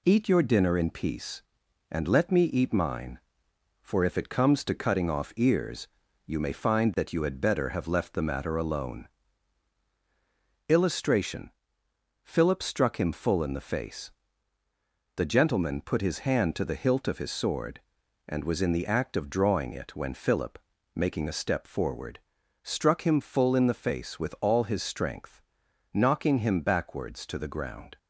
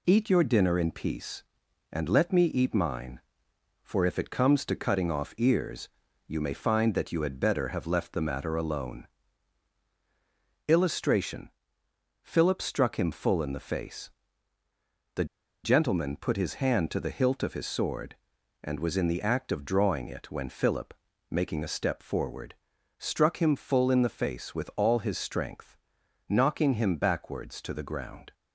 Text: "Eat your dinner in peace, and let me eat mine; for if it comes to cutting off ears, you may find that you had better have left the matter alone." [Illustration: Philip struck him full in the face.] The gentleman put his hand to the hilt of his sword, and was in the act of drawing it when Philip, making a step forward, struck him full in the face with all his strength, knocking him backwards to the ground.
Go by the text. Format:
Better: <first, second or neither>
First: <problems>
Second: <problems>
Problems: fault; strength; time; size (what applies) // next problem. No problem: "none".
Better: first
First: none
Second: pauses between "The" and "gentleman"; at 15.2 s; 0.39 s long